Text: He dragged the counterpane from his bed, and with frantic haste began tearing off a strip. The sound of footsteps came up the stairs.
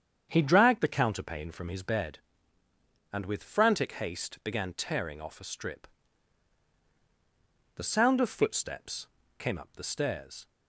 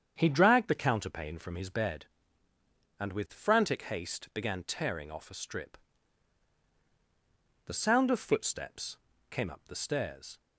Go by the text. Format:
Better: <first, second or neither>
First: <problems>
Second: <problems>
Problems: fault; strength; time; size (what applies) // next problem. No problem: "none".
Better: neither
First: starts louder than the rest; strong; until 1.3 s; 8 dB // pauses between "footsteps" and "came"; slight; at 9.0 s; 0.30 s long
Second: starts louder than the rest; strong; until 1.1 s; 8 dB // pauses between "footsteps" and "came"; slight; at 8.9 s; 0.32 s long